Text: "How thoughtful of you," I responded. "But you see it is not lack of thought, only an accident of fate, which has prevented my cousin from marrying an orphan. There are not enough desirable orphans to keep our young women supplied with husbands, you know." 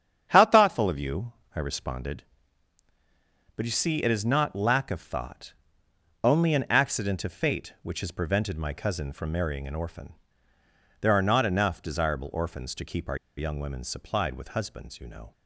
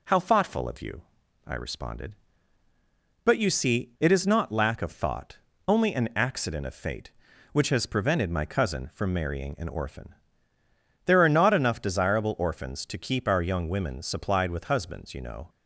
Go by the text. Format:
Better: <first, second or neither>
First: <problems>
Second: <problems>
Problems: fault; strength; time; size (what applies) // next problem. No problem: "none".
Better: second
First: starts louder than the rest; strong; until 1.3 s; 8.5 dB // pauses between "our" and "young"; slight; at 13.1 s; 0.20 s long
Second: none